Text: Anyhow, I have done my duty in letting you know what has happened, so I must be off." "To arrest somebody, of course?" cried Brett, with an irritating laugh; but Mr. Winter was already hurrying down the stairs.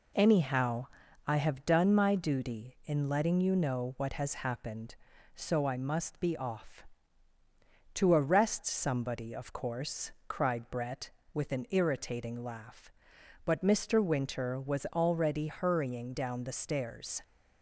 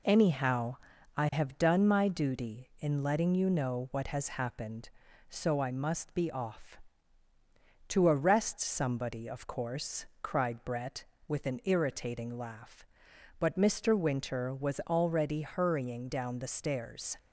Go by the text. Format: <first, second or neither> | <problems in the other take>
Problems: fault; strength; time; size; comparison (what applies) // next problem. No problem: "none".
neither | none